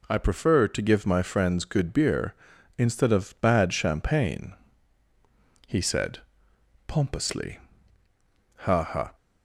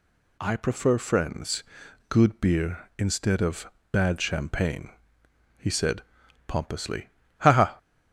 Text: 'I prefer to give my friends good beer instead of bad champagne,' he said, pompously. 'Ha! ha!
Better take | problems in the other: first | skips "to give my"; at 0.9 s // pauses between "friends" and "good"; at 1.6 s; 0.44 s long // pauses between "of" and "bad"; slight; at 3.6 s; 0.24 s long

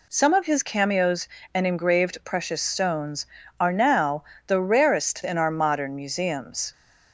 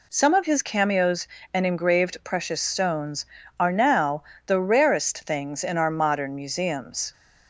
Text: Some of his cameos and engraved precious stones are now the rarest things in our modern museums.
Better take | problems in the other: second | pauses between "now" and "the"; slight; at 4.2 s; 0.22 s long; slight in the second // skips "things"; at 5.2 s

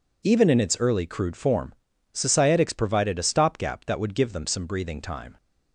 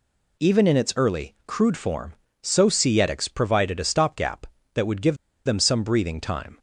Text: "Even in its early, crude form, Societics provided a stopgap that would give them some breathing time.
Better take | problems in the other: first | pauses between "give" and "them"; slight; at 5.1 s; 0.30 s long

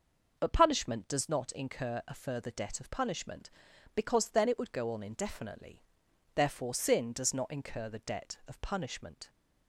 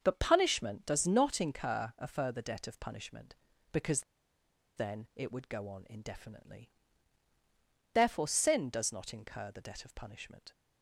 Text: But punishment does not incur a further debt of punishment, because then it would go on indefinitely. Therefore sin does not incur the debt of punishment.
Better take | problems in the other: first | starts louder than the rest; until 1.0 s; 6.5 dB; noticeable in the first // pauses between "because" and "then"; noticeable; at 4.0 s; 0.75 s long

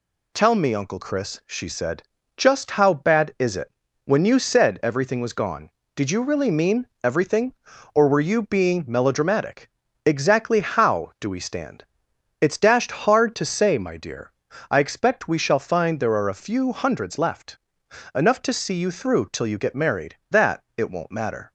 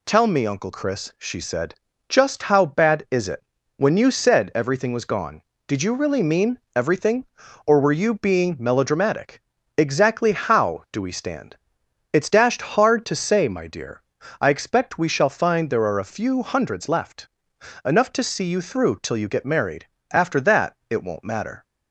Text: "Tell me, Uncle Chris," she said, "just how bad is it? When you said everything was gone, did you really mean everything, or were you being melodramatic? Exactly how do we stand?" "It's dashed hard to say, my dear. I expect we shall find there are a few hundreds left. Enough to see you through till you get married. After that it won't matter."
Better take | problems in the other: second | pauses between "mean" and "everything"; slight; at 6.8 s; 0.16 s long; slight in the second // skips "After"; at 20.2 s

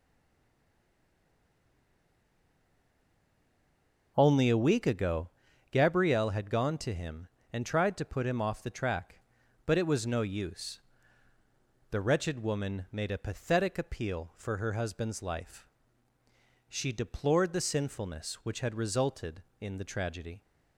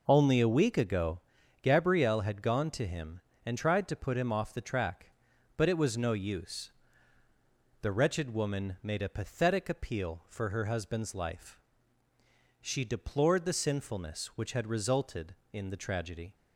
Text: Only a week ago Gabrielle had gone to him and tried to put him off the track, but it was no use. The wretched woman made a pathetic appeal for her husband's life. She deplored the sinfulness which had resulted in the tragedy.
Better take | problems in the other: second | stays silent before the first word; strong; until 4.1 s; 4.1 s long // pauses between "ago" and "Gabrielle"; at 5.3 s; 0.42 s long; also in the second

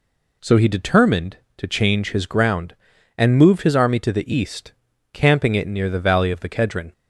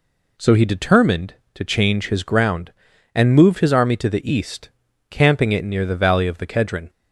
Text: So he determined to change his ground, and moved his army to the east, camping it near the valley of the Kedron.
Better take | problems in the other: neither | none

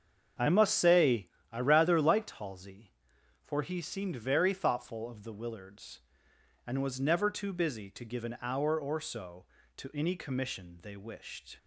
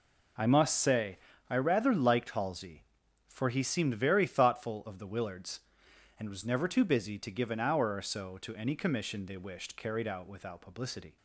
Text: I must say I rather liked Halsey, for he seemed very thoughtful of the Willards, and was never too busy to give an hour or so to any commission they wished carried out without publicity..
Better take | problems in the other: second | starts louder than the rest; until 1.6 s; 7 dB // pauses between "say" and "I"; slight; at 1.2 s; 0.22 s long; slight in the second // stops before "carried out without publicity"; at 11.5 s

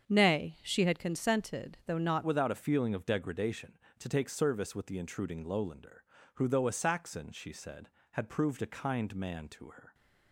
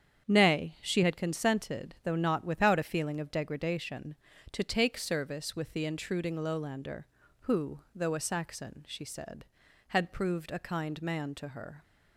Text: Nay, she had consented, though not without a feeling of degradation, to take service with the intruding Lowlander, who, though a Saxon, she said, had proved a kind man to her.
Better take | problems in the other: second | starts louder than the rest; strong; until 1.0 s; 7.5 dB; strong in the second // changes voice at "without"; from 2.2 s on; 7.7 s long

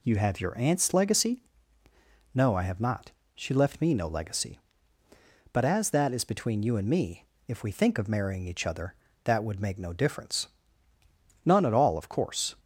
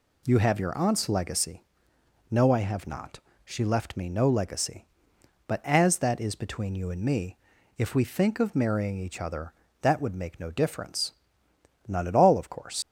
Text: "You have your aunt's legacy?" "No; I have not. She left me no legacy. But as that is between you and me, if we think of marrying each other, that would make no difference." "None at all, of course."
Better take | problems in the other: first | leaves "course" unfinished; at 12.8 s; 120 ms

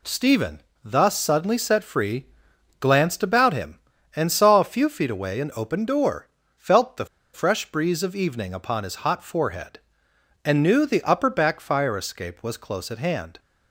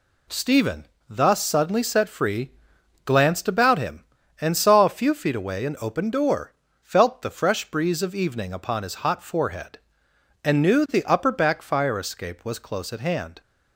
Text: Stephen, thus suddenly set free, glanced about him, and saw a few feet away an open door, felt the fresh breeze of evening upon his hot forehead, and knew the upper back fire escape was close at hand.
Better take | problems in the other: second | pauses between "the" and "fresh"; slight; at 7.0 s; 0.28 s long

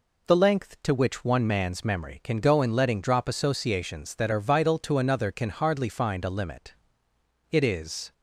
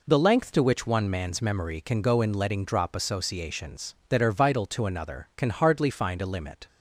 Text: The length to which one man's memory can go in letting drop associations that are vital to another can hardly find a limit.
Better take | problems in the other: second | goes on to say "It is"; noticeable; from 7.5 s on; 0.62 s long

